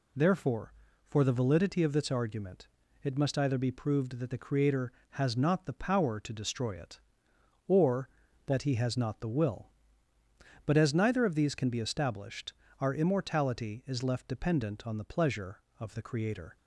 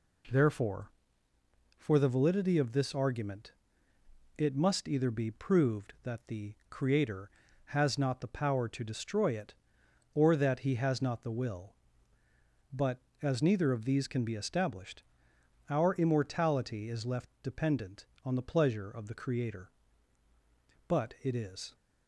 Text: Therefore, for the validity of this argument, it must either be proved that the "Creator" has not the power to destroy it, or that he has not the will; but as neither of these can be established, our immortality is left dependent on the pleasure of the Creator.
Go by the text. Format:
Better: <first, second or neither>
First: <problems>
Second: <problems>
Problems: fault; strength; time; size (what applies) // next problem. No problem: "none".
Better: first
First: none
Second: goes on to say "But it is"; noticeable; from 20.8 s on; 0.88 s long